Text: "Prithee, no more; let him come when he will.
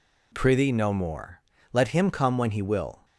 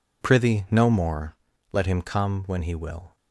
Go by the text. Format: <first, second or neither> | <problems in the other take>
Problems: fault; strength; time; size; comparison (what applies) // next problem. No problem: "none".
neither | none